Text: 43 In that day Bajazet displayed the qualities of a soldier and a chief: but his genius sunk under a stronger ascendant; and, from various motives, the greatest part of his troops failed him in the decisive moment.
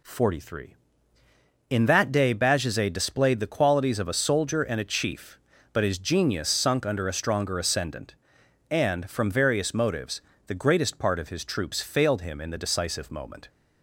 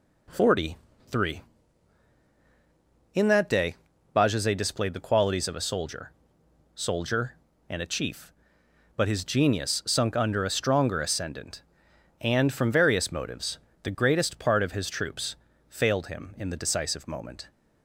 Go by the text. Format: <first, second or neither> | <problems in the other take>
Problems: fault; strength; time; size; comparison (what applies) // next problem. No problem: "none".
first | pauses between "day" and "Bajazet"; at 3.7 s; 0.40 s long // says "soldier" twice; at 6.7 s // pauses between "troops" and "failed"; slight; at 15.3 s; 0.34 s long